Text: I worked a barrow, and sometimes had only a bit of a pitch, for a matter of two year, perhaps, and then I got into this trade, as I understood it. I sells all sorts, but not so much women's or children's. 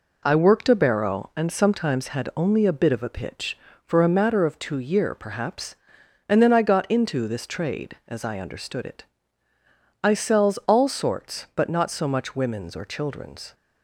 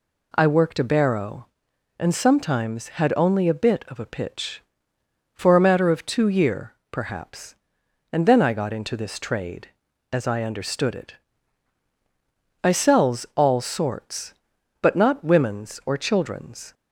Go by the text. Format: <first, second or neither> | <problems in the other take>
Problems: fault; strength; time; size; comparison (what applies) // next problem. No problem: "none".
first | skips "so much"; at 15.2 s